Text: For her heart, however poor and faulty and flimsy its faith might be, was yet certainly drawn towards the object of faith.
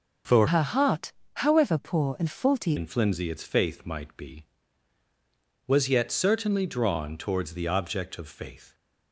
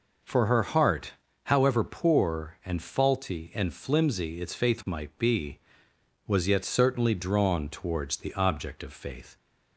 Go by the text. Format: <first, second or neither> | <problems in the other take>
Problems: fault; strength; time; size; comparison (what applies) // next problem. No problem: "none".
second | changes voice from "her" to "faulty"; from 0.4 to 2.7 s; 2.3 s long